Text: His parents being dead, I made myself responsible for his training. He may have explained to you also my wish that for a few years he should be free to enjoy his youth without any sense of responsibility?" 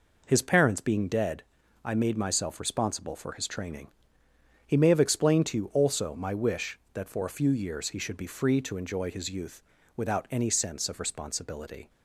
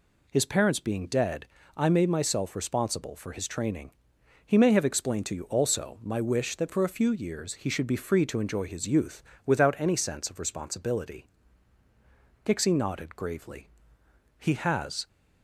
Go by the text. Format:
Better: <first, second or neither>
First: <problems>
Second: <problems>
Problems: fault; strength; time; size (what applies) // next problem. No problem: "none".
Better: first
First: pauses between "youth" and "without"; slight; at 9.6 s; 0.34 s long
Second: pauses between "youth" and "without"; slight; at 9.2 s; 0.24 s long // goes on to say "Pixie nodded gravely He has"; strong; from 12.4 s on; 2.6 s long